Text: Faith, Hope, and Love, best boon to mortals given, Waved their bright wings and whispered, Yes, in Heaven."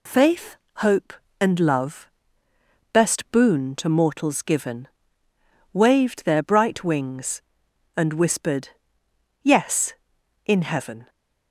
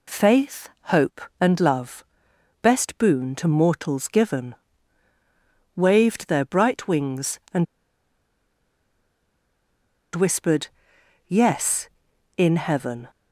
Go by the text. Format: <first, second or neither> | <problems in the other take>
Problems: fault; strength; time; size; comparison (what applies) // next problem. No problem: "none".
first | pauses between "and" and "whispered"; strong; at 7.6 s; 2.5 s long